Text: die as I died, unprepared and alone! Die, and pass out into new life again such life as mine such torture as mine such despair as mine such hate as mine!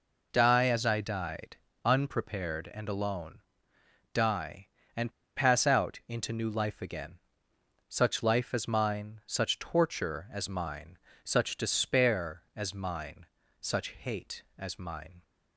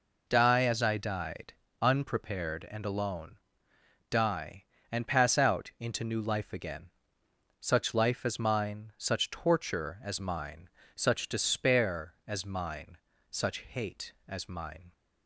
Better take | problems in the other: second | pauses between "and" and "pass"; slight; at 5.1 s; 0.24 s long // pauses between "again" and "such"; noticeable; at 7.1 s; 0.68 s long; noticeable in the second // pauses between "mine" and "such"; slight; at 10.9 s; 0.26 s long; slight in the second // pauses between "mine" and "such"; slight; at 13.2 s; 0.34 s long; slight in the second

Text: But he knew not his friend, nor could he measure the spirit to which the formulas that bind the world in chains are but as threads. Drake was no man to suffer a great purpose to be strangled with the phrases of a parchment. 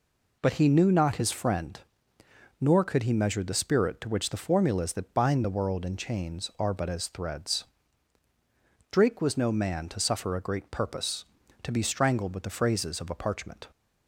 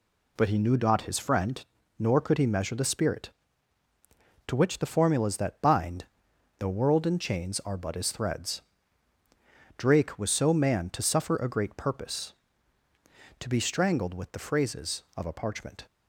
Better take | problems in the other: first | pauses between "bind" and "the"; noticeable; at 6.0 s; 0.54 s long // says "so" for "no"; at 10.3 s

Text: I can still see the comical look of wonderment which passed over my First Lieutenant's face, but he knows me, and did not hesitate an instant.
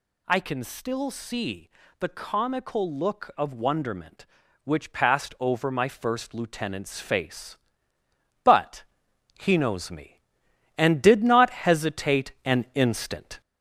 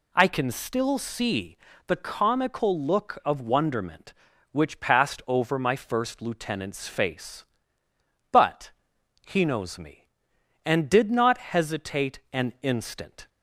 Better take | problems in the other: second | gets louder; throughout; 3.5 dB // pauses between "see" and "the"; slight; at 1.6 s; 0.30 s long; slight in the second // pauses between "but" and "he"; noticeable; at 8.8 s; 0.56 s long; noticeable in the second

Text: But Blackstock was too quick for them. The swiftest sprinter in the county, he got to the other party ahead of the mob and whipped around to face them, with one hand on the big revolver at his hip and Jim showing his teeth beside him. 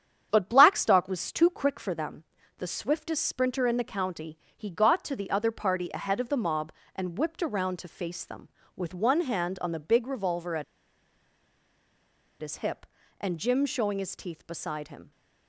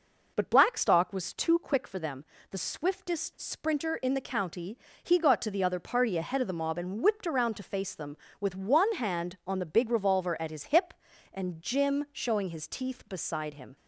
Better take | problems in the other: second | starts louder than the rest; strong; until 1.3 s; 8.5 dB // pauses between "at" and "his"; strong; at 10.6 s; 1.7 s long

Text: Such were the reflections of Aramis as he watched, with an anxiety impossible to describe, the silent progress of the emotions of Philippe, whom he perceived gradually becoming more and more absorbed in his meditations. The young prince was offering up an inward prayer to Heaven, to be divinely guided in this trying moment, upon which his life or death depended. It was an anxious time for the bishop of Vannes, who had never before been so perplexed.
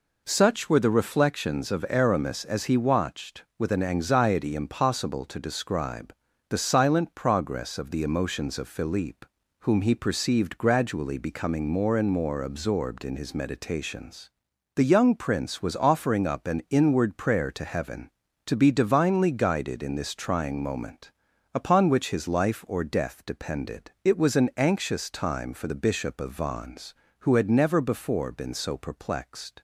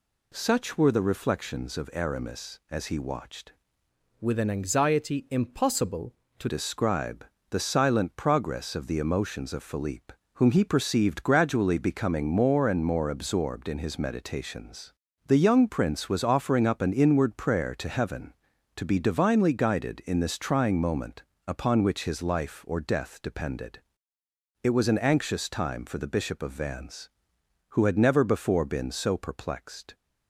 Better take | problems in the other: first | changes voice from "with" to "to"; from 4.1 to 6.4 s; 2.3 s long

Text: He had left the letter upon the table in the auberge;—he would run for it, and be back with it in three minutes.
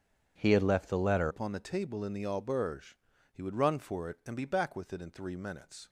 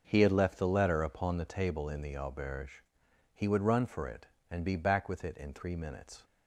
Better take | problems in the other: second | starts louder than the rest; strong; until 1.3 s; 8 dB; noticeable in the second // changes voice at "upon"; from 1.2 s on; 4.6 s long

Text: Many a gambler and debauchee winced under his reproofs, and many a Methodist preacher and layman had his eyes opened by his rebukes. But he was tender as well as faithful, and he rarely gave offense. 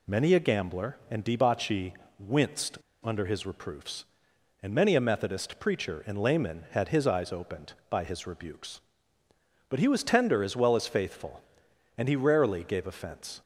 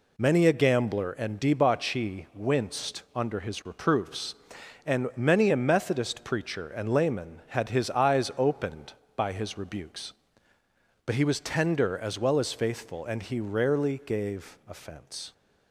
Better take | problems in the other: second | pauses between "debauchee" and "winced"; slight; at 1.9 s; 0.24 s long // pauses between "winced" and "under"; slight; at 2.7 s; 0.26 s long

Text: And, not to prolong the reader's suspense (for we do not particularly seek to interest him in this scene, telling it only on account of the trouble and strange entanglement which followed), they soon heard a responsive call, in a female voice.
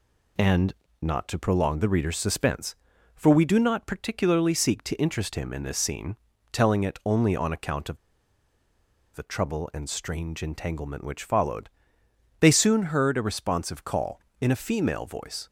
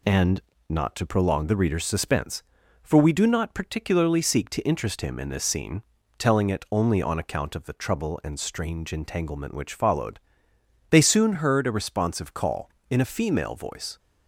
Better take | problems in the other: second | pauses between "of" and "the"; at 7.9 s; 1.1 s long

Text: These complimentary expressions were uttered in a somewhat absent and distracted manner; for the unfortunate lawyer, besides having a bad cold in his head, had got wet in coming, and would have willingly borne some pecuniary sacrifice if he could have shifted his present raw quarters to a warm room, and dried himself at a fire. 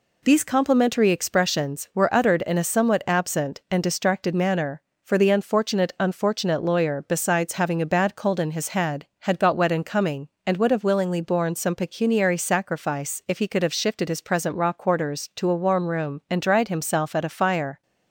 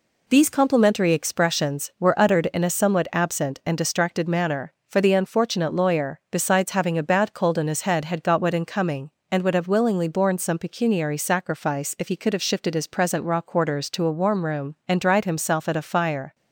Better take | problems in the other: second | says "unfortunate" twice; at 5.9 s

